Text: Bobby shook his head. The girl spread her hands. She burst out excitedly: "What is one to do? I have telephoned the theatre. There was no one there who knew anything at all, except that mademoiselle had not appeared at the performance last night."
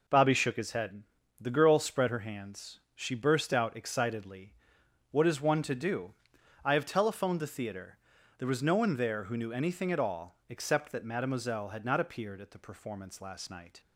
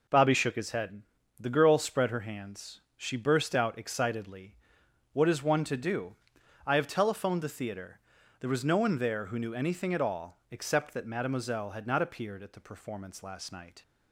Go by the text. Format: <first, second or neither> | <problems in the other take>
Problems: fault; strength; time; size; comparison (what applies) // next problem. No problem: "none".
neither | none